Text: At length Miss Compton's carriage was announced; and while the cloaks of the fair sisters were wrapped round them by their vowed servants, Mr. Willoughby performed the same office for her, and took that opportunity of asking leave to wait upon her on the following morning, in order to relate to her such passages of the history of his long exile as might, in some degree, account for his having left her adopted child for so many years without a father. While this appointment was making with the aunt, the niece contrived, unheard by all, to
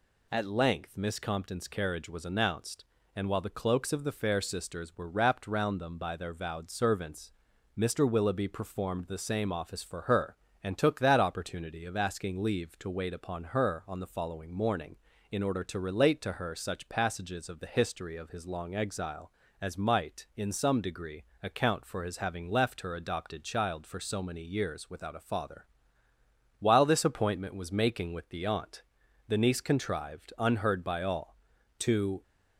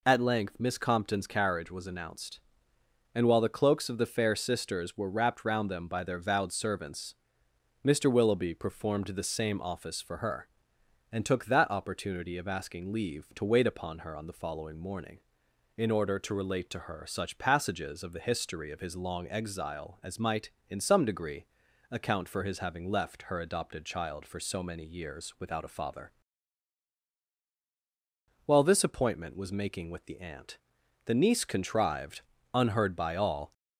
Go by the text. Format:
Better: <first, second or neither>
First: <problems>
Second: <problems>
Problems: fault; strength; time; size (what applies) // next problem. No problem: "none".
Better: first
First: none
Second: stops before "to"; at 33.5 s